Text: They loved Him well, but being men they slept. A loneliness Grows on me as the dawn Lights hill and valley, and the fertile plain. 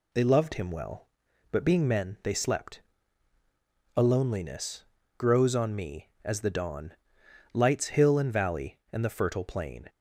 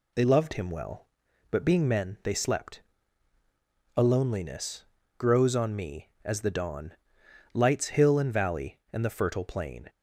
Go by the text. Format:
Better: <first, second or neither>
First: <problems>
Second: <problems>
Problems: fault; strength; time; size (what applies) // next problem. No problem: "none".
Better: neither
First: pauses between "loneliness" and "Grows"; slight; at 4.8 s; 0.34 s long // pauses between "dawn" and "Lights"; noticeable; at 6.9 s; 0.60 s long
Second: pauses between "loneliness" and "Grows"; slight; at 4.8 s; 0.34 s long // pauses between "dawn" and "Lights"; noticeable; at 6.9 s; 0.60 s long